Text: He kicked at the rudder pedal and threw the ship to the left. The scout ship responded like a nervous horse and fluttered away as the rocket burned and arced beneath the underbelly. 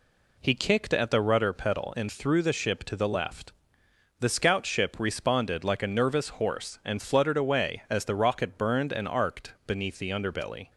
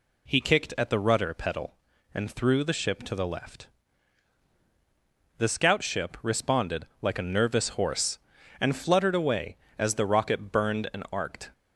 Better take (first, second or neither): first